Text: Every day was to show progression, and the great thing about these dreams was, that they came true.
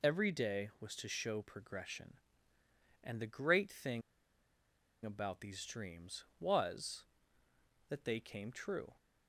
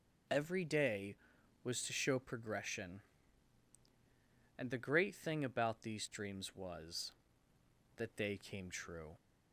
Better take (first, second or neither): second